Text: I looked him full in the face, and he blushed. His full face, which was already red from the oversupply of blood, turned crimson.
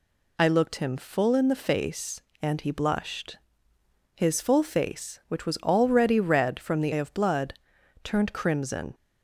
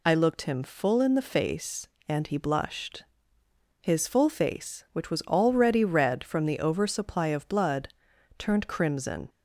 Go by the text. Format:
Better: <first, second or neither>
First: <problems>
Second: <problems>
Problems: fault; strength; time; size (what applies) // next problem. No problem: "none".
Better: second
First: skips "oversupply"; at 6.9 s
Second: none